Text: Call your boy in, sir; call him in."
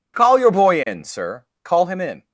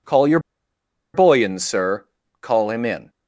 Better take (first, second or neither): first